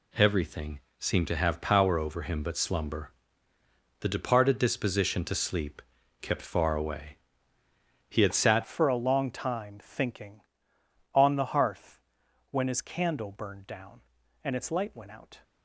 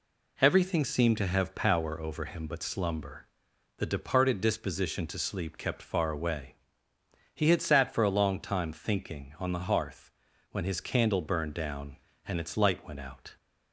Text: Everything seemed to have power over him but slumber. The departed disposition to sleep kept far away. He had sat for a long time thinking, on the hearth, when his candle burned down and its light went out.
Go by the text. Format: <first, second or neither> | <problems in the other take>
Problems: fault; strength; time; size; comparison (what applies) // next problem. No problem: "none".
second | pauses between "Everything" and "seemed"; slight; at 0.8 s; 0.18 s long // pauses between "sleep" and "kept"; at 5.8 s; 0.38 s long // changes voice at "for"; from 8.6 s on; 6.8 s long